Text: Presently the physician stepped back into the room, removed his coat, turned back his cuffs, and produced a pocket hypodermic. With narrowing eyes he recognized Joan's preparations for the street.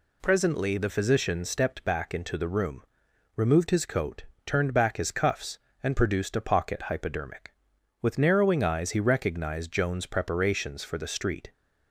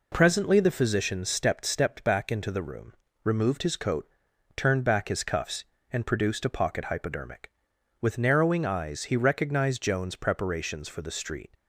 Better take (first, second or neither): first